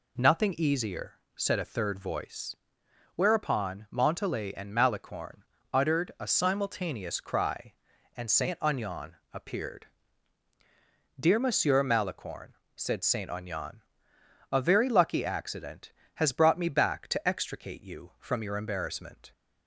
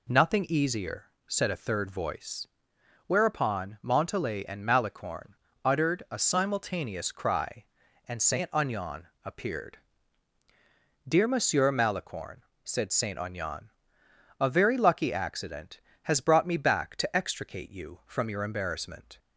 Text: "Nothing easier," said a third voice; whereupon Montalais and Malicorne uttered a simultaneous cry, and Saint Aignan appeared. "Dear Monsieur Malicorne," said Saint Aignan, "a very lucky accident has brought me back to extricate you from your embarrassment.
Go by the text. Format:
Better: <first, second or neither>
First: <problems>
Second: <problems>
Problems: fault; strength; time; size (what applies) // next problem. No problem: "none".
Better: neither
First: pauses between "Malicorne" and "uttered"; slight; at 5.4 s; 0.32 s long // pauses between "Aignan" and "appeared"; slight; at 9.1 s; 0.18 s long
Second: pauses between "Malicorne" and "uttered"; slight; at 5.3 s; 0.32 s long // pauses between "Aignan" and "appeared"; slight; at 9.0 s; 0.18 s long